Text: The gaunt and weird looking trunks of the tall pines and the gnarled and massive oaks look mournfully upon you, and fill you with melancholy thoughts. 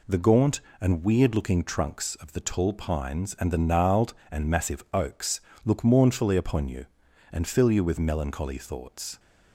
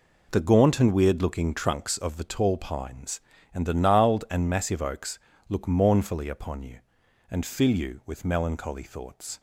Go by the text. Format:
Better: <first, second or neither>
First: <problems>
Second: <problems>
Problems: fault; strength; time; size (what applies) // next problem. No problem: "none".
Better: first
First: pauses between "oaks" and "look"; slight; at 5.3 s; 0.24 s long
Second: gets quieter; strong; throughout; 9.5 dB // pauses between "oaks" and "look"; slight; at 5.1 s; 0.30 s long